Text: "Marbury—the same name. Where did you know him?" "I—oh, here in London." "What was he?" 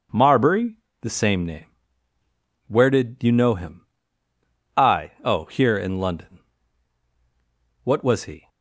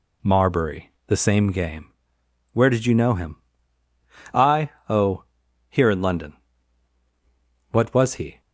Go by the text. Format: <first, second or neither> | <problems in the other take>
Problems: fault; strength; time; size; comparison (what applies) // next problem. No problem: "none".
first | says "game" for "name"; at 1.5 s